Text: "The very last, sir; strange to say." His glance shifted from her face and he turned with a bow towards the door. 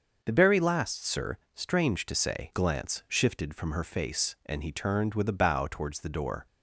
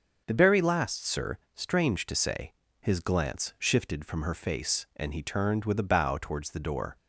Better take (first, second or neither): second